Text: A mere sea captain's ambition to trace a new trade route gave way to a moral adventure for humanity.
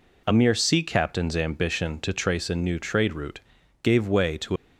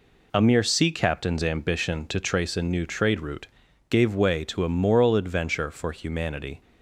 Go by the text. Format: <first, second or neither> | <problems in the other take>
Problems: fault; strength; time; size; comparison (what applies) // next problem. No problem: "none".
second | pauses between "route" and "gave"; at 3.3 s; 0.42 s long; also in the second // stops before "a moral adventure for humanity"; at 4.5 s